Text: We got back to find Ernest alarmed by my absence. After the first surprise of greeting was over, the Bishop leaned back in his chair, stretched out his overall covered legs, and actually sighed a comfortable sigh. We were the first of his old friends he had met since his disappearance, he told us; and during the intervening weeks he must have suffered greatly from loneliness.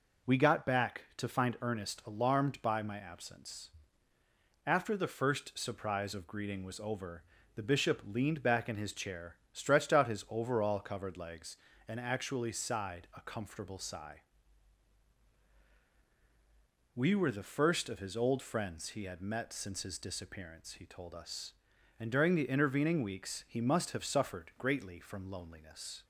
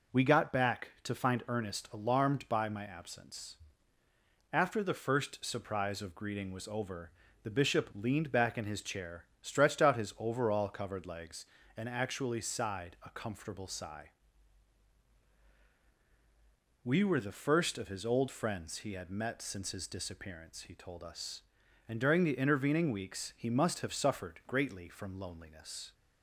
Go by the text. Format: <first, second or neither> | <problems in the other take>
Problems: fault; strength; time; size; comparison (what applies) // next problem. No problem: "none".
neither | none